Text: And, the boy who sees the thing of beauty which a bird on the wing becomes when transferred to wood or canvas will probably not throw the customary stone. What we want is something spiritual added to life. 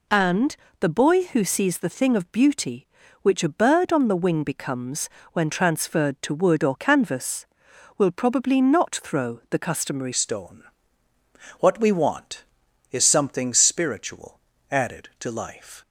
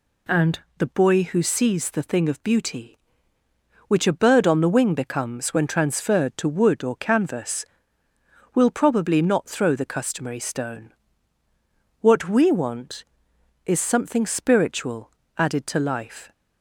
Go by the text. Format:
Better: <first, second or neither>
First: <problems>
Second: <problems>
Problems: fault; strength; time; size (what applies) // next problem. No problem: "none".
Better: second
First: pauses between "becomes" and "when"; slight; at 5.0 s; 0.24 s long // changes voice at "stone"; from 10.1 s on; 5.6 s long // pauses between "spiritual" and "added"; slight; at 14.3 s; 0.32 s long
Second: pauses between "spiritual" and "added"; slight; at 15.1 s; 0.26 s long